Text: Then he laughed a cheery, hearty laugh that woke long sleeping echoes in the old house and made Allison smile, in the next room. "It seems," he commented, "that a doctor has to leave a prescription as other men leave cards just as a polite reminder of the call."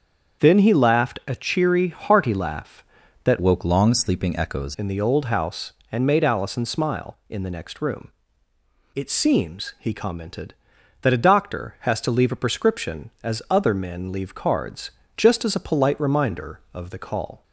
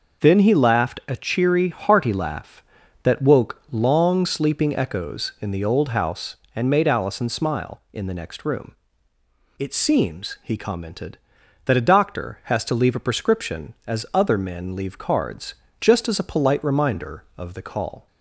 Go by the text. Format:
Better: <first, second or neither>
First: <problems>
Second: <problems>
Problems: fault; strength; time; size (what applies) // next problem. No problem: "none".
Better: second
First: starts louder than the rest; until 1.4 s; 7 dB // changes voice from "woke" to "echoes"; from 3.3 to 4.7 s; 1.4 s long // pauses between "cards" and "just"; slight; at 14.9 s; 0.26 s long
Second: pauses between "cards" and "just"; slight; at 15.5 s; 0.26 s long